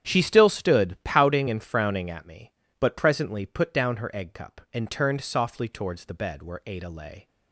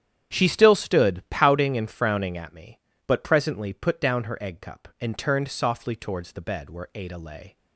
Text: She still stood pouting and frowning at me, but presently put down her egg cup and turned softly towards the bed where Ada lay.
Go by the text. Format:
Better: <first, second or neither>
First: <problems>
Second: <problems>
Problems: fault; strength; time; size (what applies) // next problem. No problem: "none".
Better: neither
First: starts louder than the rest; strong; until 1.1 s; 9.5 dB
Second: starts louder than the rest; strong; until 1.3 s; 9.5 dB